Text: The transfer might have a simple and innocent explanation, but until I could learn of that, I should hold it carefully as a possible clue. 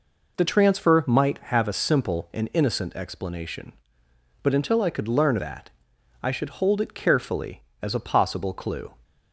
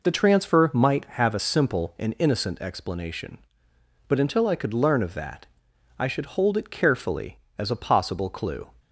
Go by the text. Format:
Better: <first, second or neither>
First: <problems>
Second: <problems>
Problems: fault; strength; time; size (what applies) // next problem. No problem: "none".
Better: second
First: skips "of"; at 5.3 s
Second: none